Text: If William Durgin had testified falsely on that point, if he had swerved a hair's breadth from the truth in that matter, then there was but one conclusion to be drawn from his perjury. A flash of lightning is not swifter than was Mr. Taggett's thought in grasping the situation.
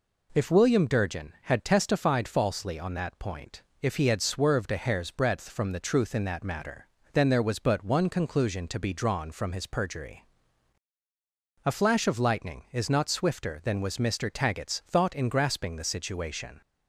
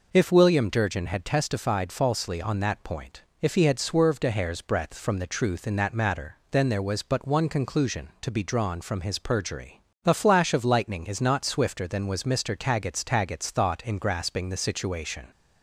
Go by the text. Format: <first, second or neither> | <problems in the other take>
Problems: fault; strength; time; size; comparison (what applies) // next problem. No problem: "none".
first | says "Taggett's" twice; at 13.0 s